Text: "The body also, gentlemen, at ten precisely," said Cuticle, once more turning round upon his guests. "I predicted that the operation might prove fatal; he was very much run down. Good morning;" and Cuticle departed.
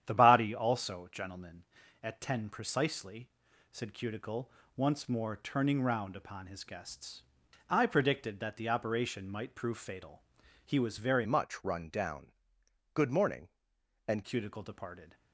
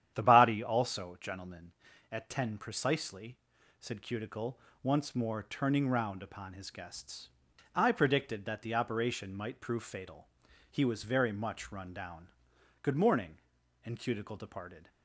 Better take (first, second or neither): second